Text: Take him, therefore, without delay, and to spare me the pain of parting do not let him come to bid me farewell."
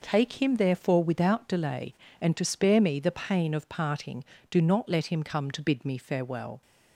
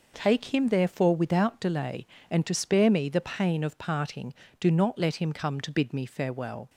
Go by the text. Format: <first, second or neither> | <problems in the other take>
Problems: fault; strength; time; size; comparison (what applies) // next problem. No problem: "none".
neither | none